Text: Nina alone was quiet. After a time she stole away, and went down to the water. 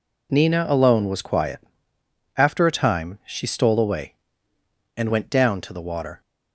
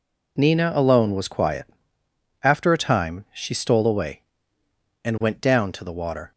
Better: neither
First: none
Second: none

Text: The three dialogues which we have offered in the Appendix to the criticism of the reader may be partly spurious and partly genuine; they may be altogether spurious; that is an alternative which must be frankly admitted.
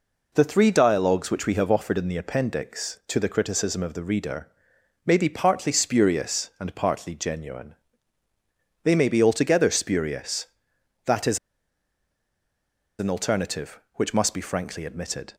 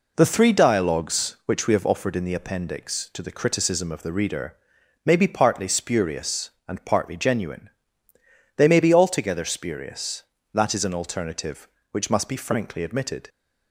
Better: second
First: pauses between "reader" and "may"; noticeable; at 4.4 s; 0.56 s long // pauses between "is" and "an"; strong; at 11.3 s; 1.6 s long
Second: pauses between "reader" and "may"; noticeable; at 4.5 s; 0.50 s long

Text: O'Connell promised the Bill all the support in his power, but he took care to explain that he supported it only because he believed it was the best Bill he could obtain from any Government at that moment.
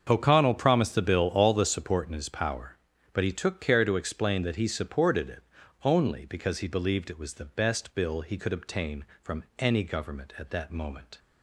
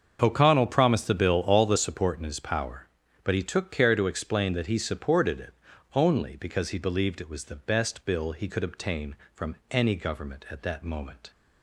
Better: neither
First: starts louder than the rest; until 1.1 s; 7 dB // pauses between "it" and "only"; at 5.4 s; 0.42 s long // pauses between "from" and "any"; slight; at 9.4 s; 0.16 s long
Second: starts louder than the rest; until 1.2 s; 7 dB // pauses between "it" and "only"; at 5.5 s; 0.42 s long // pauses between "from" and "any"; slight; at 9.5 s; 0.16 s long

